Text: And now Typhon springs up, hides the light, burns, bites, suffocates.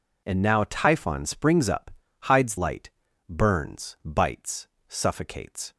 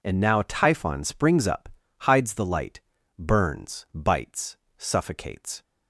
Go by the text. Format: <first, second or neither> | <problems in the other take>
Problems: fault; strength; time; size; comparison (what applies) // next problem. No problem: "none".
second | skips "the"; at 2.5 s